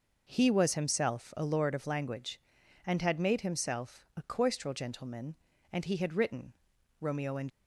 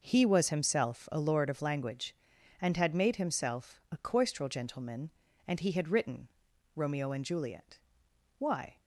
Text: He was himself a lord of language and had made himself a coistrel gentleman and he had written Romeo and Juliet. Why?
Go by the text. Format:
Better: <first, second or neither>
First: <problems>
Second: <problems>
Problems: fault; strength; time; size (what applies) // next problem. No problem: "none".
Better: second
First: pauses between "written" and "Romeo"; noticeable; at 6.5 s; 0.48 s long // stops before "Juliet Why"; at 7.4 s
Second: pauses between "written" and "Romeo"; noticeable; at 6.2 s; 0.48 s long